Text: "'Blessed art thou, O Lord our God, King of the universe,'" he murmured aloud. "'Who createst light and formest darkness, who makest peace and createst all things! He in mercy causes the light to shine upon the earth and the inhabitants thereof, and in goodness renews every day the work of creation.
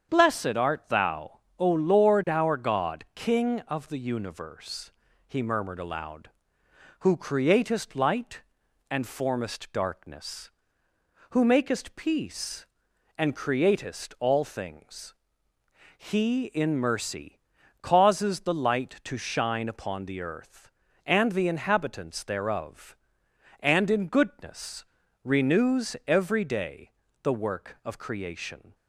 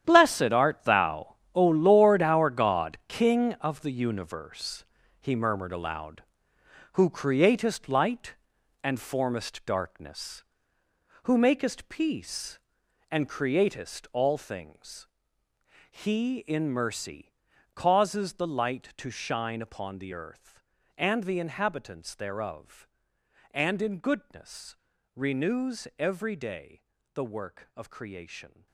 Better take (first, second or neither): first